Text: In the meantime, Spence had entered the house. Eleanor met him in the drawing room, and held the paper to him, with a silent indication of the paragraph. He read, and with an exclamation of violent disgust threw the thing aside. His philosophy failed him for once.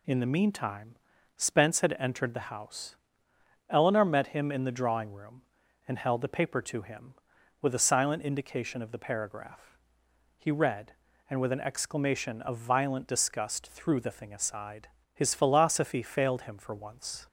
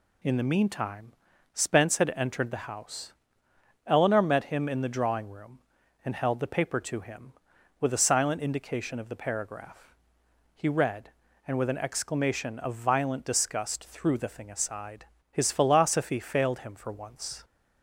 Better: neither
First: none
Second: none

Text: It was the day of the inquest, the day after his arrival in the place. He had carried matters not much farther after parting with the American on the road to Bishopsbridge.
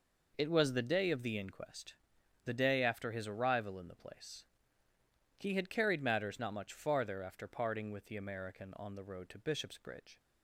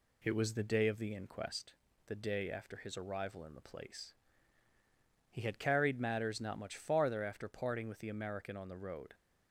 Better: first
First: none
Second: stops before "to Bishopsbridge"; at 9.1 s

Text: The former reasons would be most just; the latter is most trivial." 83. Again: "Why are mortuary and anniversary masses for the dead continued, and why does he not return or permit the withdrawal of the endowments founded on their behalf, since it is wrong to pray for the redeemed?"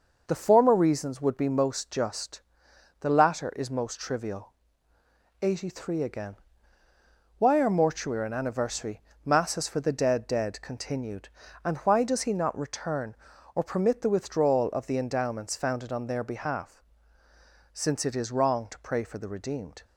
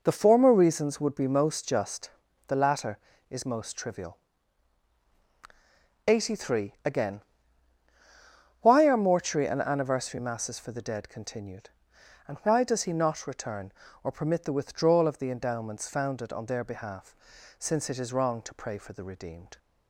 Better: second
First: pauses between "anniversary" and "masses"; slight; at 9.0 s; 0.22 s long // says "dead" twice; at 10.2 s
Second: none

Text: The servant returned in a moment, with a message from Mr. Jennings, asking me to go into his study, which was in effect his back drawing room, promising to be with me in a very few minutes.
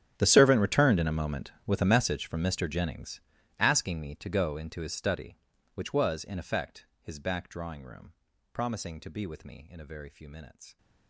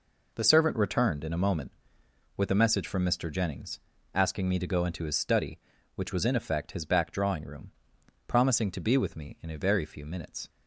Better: second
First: gets quieter; strong; throughout; 21.5 dB // pauses between "effect" and "his"; slight; at 6.8 s; 0.16 s long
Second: none

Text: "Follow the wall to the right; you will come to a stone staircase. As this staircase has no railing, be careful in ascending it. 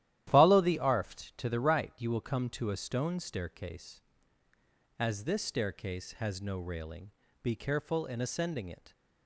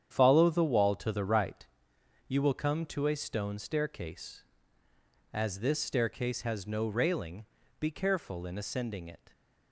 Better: second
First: starts louder than the rest; strong; until 1.3 s; 13 dB // says "arft" for "wall"; at 0.7 s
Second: starts louder than the rest; strong; until 1.2 s; 9 dB

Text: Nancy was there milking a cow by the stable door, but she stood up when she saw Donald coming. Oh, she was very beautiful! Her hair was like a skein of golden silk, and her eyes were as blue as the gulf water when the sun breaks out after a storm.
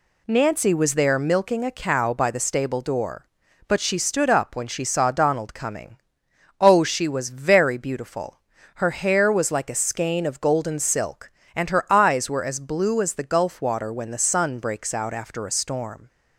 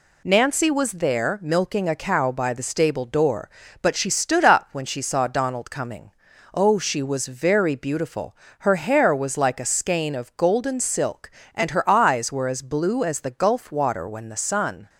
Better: first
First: none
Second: stops before "breaks out after a storm"; at 14.8 s

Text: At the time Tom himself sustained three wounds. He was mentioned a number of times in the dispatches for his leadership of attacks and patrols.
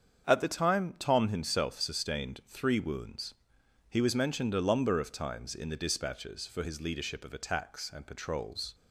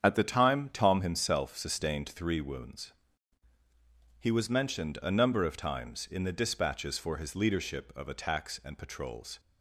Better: second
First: starts louder than the rest; strong; until 1.3 s; 7.5 dB // says "lumber" for "number"; at 4.6 s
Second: starts louder than the rest; strong; until 1.0 s; 8 dB

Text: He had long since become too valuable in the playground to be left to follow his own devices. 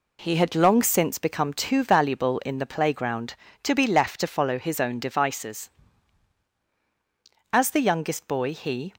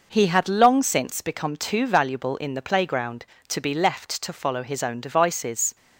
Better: second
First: goes on to say "As the youngest boy he"; from 7.5 s on; 1.3 s long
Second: none

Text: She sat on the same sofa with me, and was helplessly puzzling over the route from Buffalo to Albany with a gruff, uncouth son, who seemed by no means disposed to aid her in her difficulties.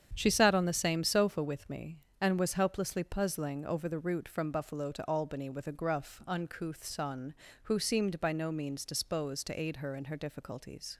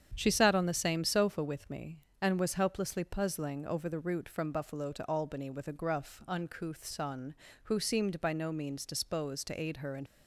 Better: first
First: starts louder than the rest; strong; until 1.1 s; 8.5 dB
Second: starts louder than the rest; strong; until 1.1 s; 8.5 dB // stops before "her difficulties"; at 10.0 s

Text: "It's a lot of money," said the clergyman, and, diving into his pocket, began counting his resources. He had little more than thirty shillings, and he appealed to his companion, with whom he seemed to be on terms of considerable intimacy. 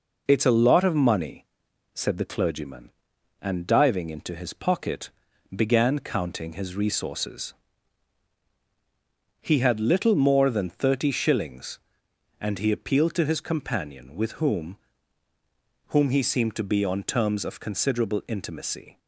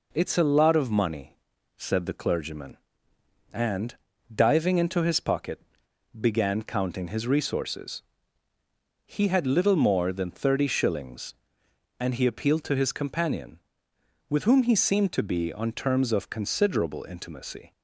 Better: second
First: says "whom" twice; at 15.8 s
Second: none

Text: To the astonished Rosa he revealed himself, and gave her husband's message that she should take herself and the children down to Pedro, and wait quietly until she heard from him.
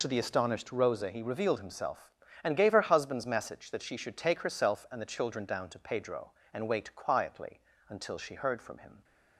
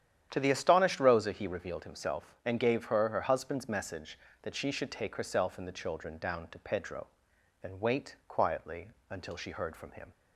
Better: first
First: pauses between "quietly" and "until"; slight; at 7.5 s; 0.28 s long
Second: starts louder than the rest; strong; until 1.3 s; 10 dB // says "her" twice; at 3.0 s // pauses between "quietly" and "until"; slight; at 8.8 s; 0.20 s long

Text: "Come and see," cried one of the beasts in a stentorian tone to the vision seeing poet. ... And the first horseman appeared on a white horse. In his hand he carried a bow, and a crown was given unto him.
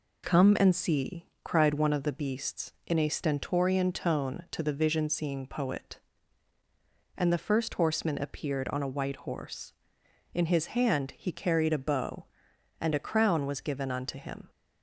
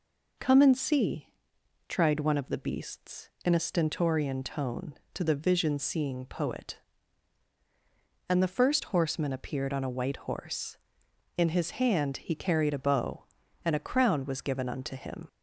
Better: first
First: none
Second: says "tried" for "cried"; at 1.8 s

